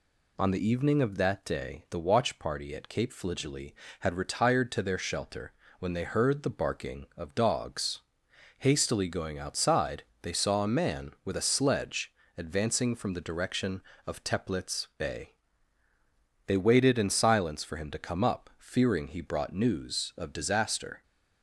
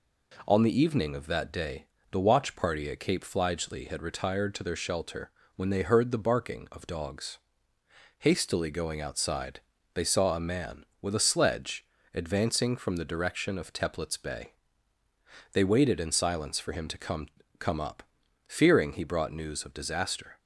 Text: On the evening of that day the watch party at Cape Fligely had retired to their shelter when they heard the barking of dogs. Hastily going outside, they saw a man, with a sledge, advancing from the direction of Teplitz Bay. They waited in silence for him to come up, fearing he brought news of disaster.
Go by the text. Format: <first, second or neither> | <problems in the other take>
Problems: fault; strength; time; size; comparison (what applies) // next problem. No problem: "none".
first | pauses between "day" and "the"; slight; at 1.8 s; 0.24 s long // pauses between "shelter" and "when"; slight; at 5.2 s; 0.26 s long; slight in the first // says "come" twice; at 17.5 s